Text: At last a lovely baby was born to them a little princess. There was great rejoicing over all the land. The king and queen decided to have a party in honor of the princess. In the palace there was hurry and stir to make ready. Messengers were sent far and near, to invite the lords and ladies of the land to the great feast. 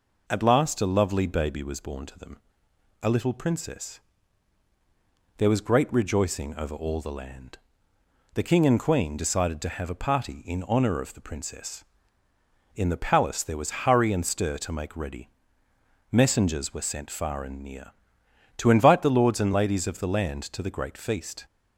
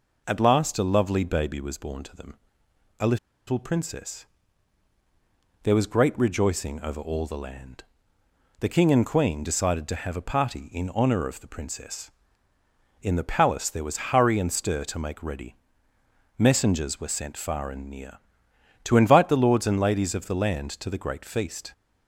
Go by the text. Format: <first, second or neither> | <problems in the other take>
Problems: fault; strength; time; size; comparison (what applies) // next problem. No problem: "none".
first | pauses between "them" and "a"; noticeable; at 2.3 s; 0.64 s long; noticeable in the first // pauses between "a" and "little"; slight; at 3.1 s; 0.31 s long